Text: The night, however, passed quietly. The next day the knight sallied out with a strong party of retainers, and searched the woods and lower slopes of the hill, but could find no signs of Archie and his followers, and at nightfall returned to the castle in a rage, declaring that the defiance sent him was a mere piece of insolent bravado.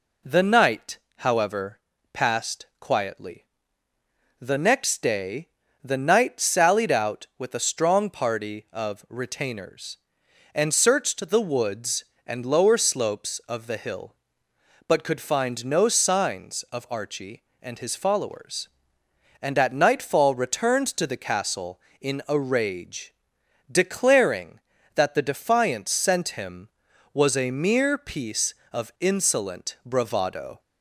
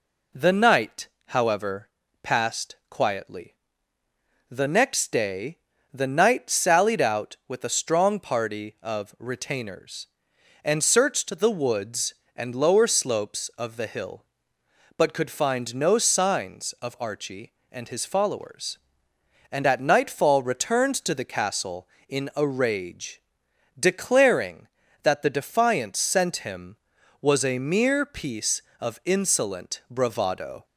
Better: neither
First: pauses between "day" and "the"; slight; at 5.4 s; 0.34 s long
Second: pauses between "day" and "the"; slight; at 5.5 s; 0.34 s long

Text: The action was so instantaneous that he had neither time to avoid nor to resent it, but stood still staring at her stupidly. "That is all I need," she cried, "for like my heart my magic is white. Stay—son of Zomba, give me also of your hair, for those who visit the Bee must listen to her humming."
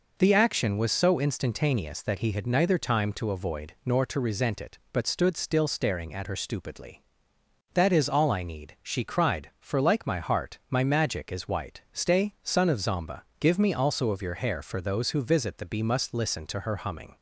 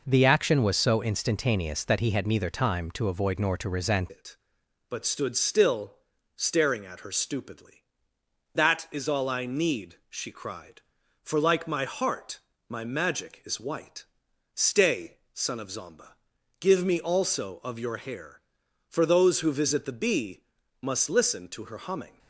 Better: first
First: none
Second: changes voice at "it"; from 4.1 s on; 18.0 s long // pauses between "still" and "staring"; at 5.9 s; 0.42 s long // pauses between "heart" and "my"; slight; at 12.4 s; 0.28 s long // pauses between "Bee" and "must"; at 20.4 s; 0.40 s long

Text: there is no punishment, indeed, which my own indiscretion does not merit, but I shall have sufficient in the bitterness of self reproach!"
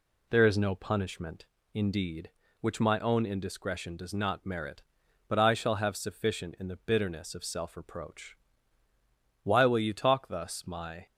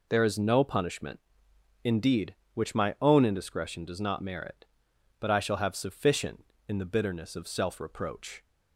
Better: second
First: goes on to say "Why will you talk thus my"; from 9.4 s on; 1.6 s long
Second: none

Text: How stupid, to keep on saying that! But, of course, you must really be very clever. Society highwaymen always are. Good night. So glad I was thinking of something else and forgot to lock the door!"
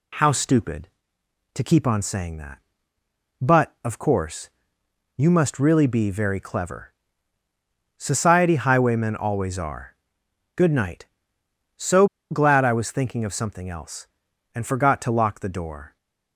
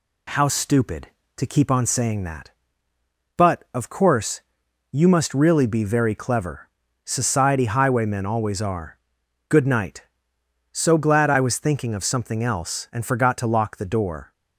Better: second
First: pauses between "So" and "glad"; slight; at 12.0 s; 0.25 s long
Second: none

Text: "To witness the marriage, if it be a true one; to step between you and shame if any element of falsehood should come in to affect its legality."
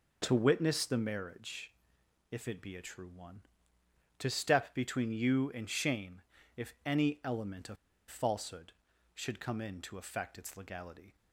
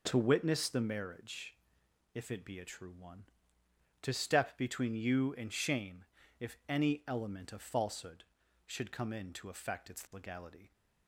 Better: second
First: pauses between "shame" and "if"; slight; at 6.2 s; 0.34 s long // pauses between "of" and "falsehood"; slight; at 7.7 s; 0.32 s long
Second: pauses between "shame" and "if"; slight; at 6.0 s; 0.34 s long

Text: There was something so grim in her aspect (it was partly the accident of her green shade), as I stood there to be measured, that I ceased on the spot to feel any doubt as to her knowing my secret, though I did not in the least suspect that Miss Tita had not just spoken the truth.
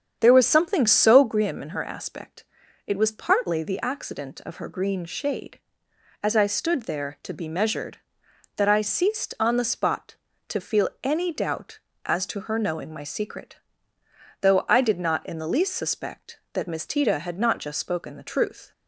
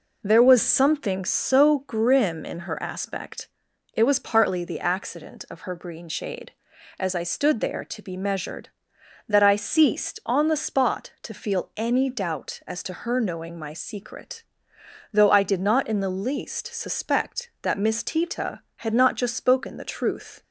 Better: second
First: starts louder than the rest; strong; until 1.4 s; 8 dB // pauses between "feel" and "any"; slight; at 10.8 s; 0.16 s long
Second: none

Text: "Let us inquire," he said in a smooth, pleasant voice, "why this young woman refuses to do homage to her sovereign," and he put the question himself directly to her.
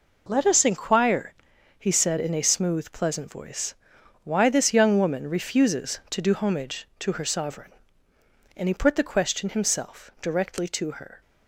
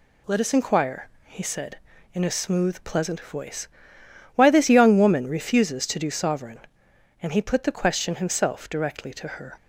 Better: first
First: none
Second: skips "homage to her"; at 6.1 s

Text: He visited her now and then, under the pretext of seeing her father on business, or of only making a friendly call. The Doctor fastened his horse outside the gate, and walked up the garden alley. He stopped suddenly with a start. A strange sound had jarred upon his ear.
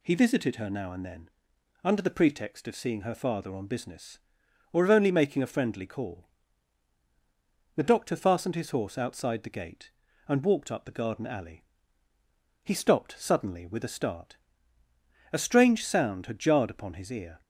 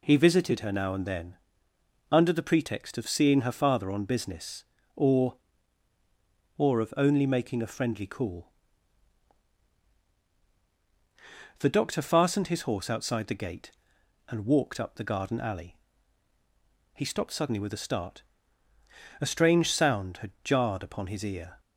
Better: first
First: none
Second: says "or" twice; at 6.5 s

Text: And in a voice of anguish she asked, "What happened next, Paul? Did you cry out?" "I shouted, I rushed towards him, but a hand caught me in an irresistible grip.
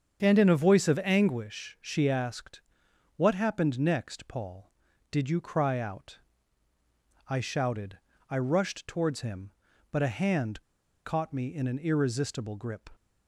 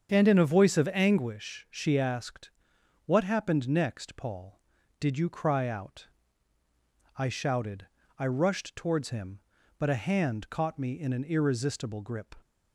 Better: second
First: starts louder than the rest; strong; until 1.2 s; 7.5 dB // pauses between "hand" and "caught"; at 10.6 s; 0.43 s long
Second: starts louder than the rest; strong; until 1.1 s; 7.5 dB

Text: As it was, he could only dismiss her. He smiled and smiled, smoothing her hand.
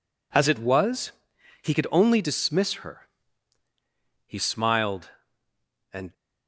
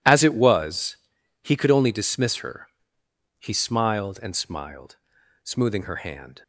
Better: second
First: stops before "smiled smoothing her hand"; at 6.1 s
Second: none

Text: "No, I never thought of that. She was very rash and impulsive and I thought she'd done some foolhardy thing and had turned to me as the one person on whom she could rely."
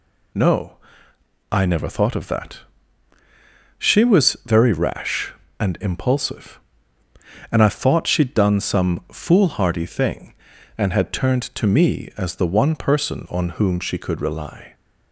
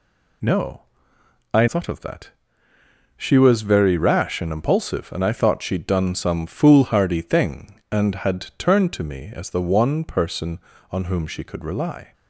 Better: first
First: none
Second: skips "never"; at 1.6 s

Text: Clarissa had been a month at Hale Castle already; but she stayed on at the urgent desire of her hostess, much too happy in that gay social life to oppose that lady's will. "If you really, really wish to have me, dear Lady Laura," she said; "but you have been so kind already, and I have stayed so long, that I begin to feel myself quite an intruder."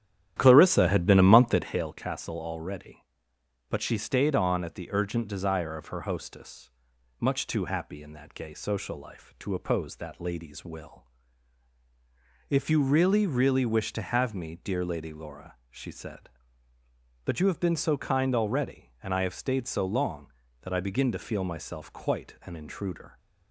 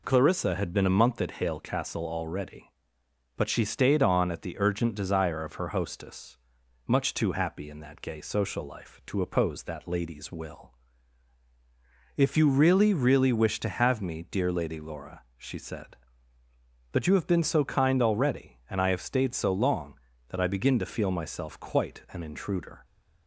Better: second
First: starts louder than the rest; strong; until 1.9 s; 11 dB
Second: none

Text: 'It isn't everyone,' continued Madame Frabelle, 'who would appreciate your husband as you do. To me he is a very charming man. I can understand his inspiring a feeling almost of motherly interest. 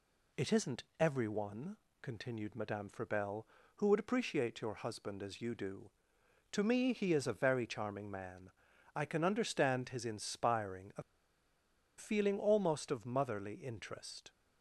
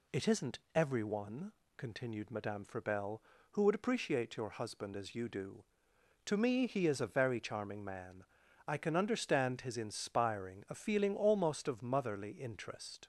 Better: second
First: pauses between "isn't" and "everyone"; slight; at 0.8 s; 0.16 s long // pauses between "a" and "feeling"; noticeable; at 11.0 s; 0.95 s long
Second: pauses between "isn't" and "everyone"; slight; at 0.5 s; 0.16 s long

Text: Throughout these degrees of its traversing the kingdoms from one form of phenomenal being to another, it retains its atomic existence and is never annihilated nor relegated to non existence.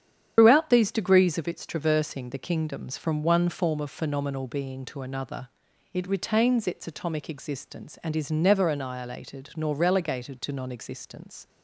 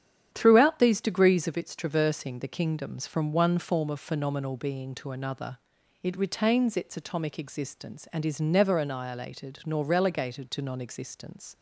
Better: second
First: loses the start of "Throughout"; at 0.3 s; 140 ms // starts louder than the rest; strong; until 1.3 s; 9.5 dB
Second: starts louder than the rest; strong; until 1.3 s; 9 dB

